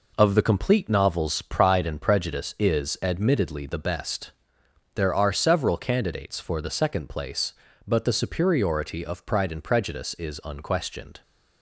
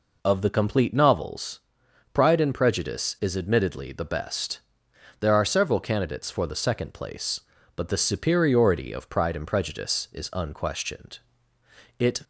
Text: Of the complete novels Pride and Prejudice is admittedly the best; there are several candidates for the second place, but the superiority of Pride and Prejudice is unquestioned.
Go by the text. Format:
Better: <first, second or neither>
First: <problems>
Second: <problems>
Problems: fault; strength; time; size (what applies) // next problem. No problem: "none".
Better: first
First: none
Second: pauses between "novels" and "Pride"; noticeable; at 1.5 s; 0.52 s long // goes on to say "It"; slight; from 11.9 s on; 0.24 s long